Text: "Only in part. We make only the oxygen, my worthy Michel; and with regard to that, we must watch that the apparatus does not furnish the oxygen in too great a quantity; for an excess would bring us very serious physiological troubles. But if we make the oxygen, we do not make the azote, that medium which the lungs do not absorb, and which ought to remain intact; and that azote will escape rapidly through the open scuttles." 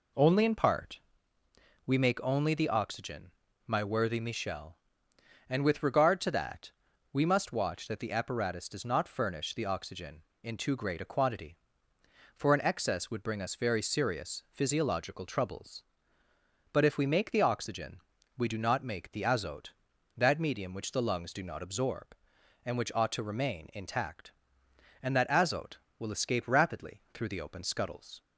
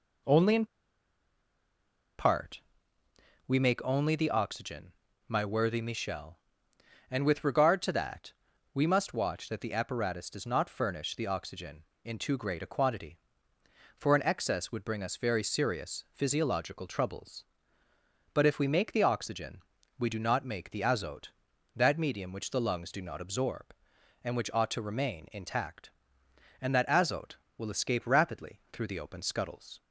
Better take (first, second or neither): first